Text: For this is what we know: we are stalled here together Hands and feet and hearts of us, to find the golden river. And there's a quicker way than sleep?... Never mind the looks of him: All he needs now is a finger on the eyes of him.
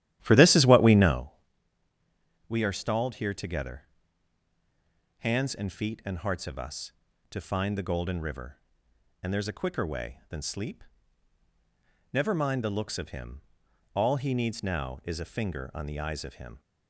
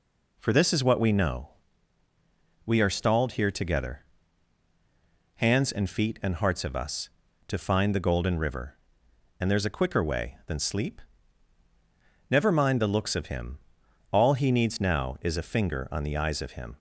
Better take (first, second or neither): second